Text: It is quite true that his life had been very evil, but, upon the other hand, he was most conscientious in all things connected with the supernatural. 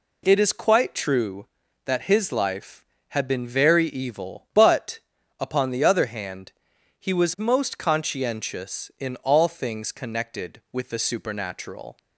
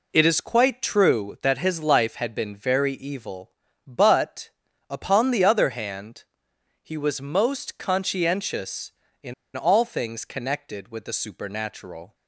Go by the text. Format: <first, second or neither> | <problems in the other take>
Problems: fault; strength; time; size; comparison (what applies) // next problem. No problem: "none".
first | pauses between "in" and "all"; slight; at 9.3 s; 0.22 s long